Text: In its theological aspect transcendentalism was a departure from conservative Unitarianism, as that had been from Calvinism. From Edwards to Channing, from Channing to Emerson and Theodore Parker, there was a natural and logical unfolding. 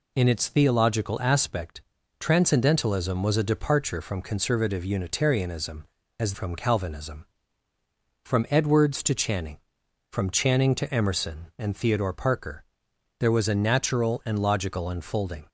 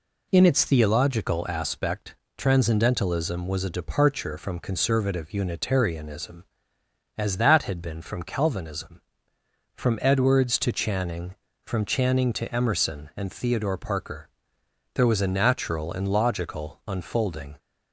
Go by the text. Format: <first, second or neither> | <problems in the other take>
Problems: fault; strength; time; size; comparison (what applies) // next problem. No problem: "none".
second | pauses between "aspect" and "transcendentalism"; at 1.8 s; 0.38 s long; slight in the second // skips "that had been"; at 6.3 s